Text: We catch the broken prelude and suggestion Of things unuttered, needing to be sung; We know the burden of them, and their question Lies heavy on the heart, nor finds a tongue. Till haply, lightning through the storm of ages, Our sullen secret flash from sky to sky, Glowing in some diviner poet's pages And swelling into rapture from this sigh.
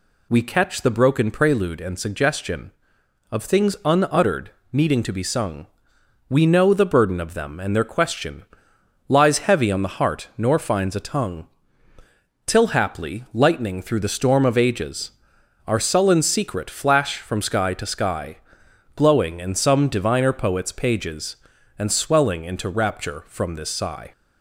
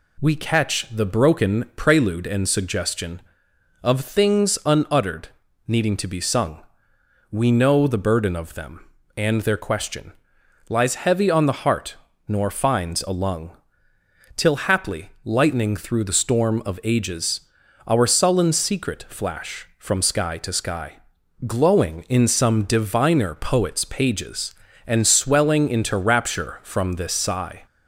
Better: first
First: pauses between "question" and "Lies"; noticeable; at 8.4 s; 0.66 s long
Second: pauses between "question" and "Lies"; noticeable; at 10.1 s; 0.58 s long // says "lung" for "tongue"; at 13.1 s

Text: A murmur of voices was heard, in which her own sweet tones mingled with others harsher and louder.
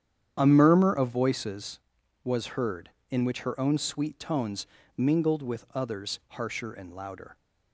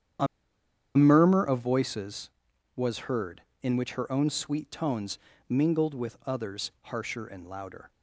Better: first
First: starts louder than the rest; strong; until 1.3 s; 9 dB // pauses between "tones" and "mingled"; slight; at 4.6 s; 0.28 s long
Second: starts louder than the rest; strong; until 1.9 s; 9 dB // pauses between "A" and "murmur"; noticeable; at 0.2 s; 0.70 s long // pauses between "tones" and "mingled"; slight; at 5.1 s; 0.28 s long

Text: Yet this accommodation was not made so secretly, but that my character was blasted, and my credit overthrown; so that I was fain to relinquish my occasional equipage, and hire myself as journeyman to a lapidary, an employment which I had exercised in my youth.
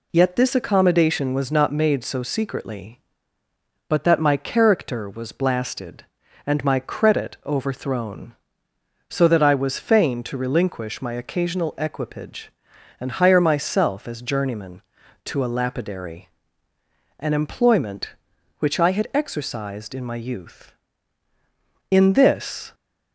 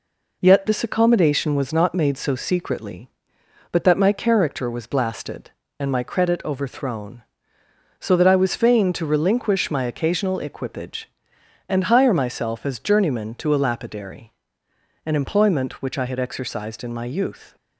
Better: second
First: goes on to say "In this"; noticeable; from 21.9 s on; 0.84 s long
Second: none

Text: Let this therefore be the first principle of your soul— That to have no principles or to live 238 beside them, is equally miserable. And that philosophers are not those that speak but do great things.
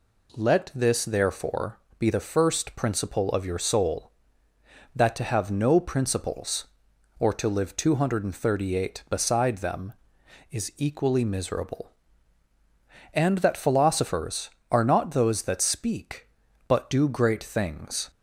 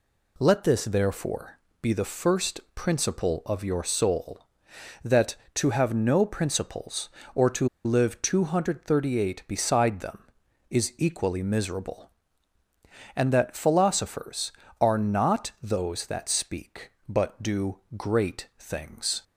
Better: first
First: pauses between "therefore" and "be"; slight; at 1.7 s; 0.20 s long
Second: pauses between "therefore" and "be"; slight; at 1.5 s; 0.24 s long // pauses between "to" and "live"; slight; at 7.6 s; 0.17 s long // pauses between "do" and "great"; slight; at 17.7 s; 0.18 s long

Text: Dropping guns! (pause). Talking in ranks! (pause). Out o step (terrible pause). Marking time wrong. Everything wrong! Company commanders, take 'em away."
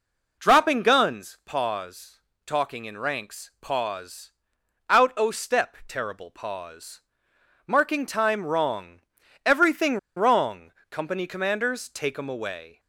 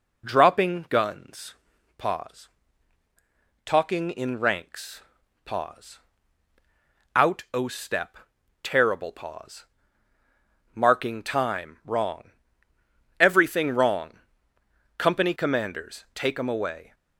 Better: second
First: pauses between "Everything" and "wrong"; slight; at 9.9 s; 0.19 s long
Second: none

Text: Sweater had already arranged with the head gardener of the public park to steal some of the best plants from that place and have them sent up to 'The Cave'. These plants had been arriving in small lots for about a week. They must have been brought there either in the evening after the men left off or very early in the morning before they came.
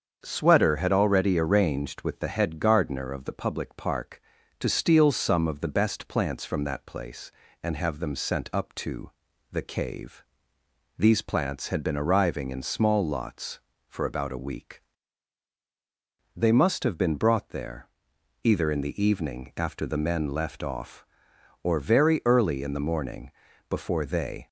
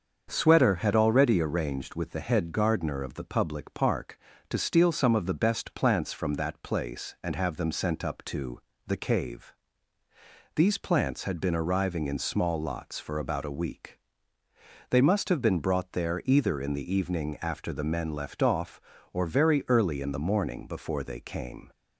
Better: second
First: starts louder than the rest; until 1.2 s; 7 dB // pauses between "to" and "The"; at 9.1 s; 0.40 s long // pauses between "there" and "either"; noticeable; at 17.8 s; 0.58 s long // pauses between "morning" and "before"; at 23.2 s; 0.40 s long // stops before "came"; at 24.4 s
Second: starts louder than the rest; until 1.3 s; 6.5 dB // pauses between "to" and "The"; slight; at 8.5 s; 0.26 s long

